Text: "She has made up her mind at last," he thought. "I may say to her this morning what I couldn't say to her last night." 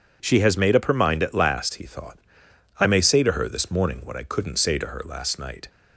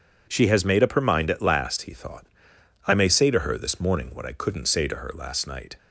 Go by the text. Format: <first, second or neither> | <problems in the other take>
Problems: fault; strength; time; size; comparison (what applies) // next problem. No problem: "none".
neither | none